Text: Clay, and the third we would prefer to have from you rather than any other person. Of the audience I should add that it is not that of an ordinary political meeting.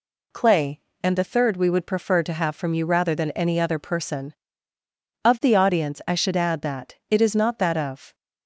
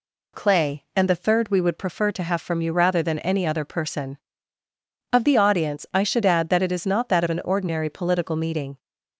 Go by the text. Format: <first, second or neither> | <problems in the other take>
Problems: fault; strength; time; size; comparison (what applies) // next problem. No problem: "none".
second | stops before "an ordinary political meeting"; at 8.1 s